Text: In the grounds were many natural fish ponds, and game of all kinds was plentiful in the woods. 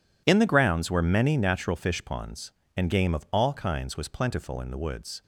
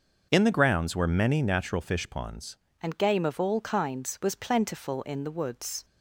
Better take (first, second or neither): first